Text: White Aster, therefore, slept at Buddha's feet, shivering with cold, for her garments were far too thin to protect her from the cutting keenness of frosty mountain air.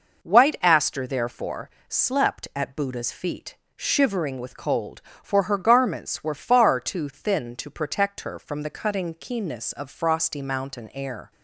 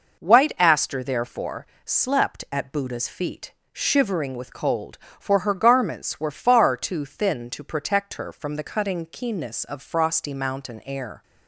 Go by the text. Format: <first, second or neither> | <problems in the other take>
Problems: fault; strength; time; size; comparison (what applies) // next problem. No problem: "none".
neither | none